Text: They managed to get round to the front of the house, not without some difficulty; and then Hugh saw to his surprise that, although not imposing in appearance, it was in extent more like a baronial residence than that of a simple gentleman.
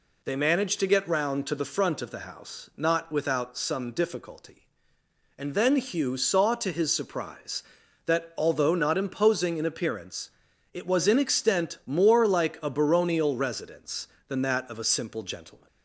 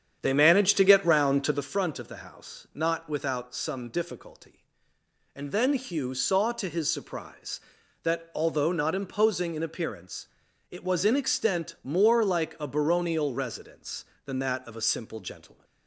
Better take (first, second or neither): first